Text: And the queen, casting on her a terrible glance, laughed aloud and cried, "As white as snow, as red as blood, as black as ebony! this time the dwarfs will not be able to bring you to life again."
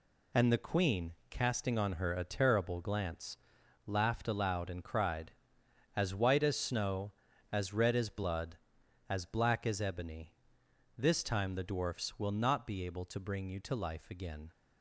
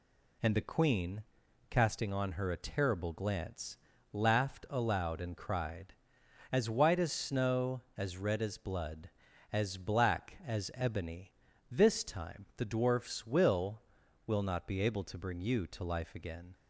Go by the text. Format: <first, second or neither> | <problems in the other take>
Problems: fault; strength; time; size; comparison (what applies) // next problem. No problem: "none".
first | says "will" twice; at 14.2 s